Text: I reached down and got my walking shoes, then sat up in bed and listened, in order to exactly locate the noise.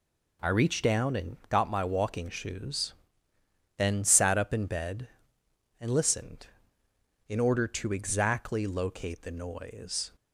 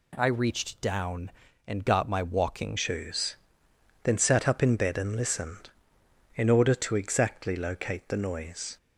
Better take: first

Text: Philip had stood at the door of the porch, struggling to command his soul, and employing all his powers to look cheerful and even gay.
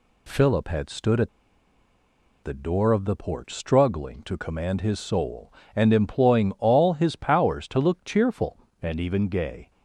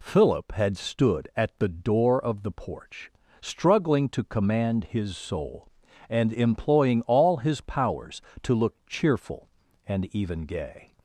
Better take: second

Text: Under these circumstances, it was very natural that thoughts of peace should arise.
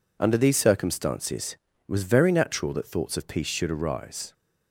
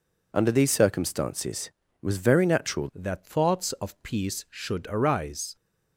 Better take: first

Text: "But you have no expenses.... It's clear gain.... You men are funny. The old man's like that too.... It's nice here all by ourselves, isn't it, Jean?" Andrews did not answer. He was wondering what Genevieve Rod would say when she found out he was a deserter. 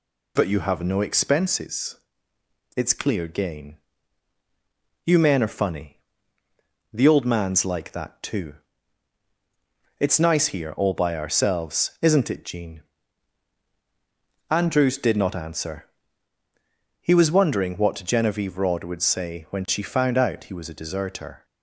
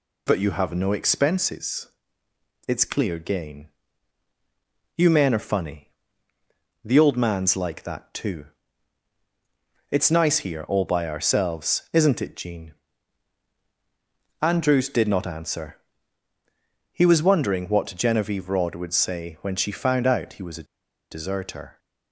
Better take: first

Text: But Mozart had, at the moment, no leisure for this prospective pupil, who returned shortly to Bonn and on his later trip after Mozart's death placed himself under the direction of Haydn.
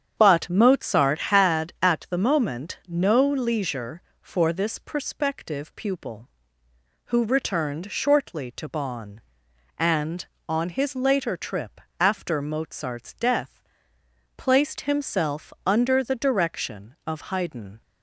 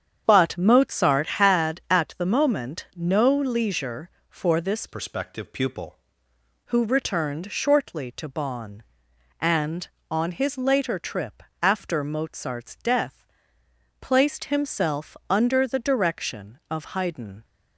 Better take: first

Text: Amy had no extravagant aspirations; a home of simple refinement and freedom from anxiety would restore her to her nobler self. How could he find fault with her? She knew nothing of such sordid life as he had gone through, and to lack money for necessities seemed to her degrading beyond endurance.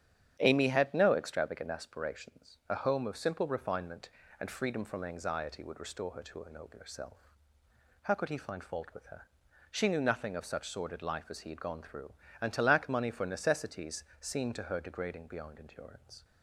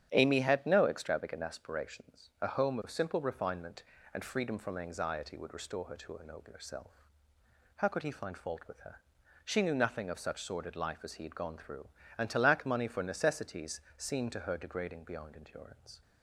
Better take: neither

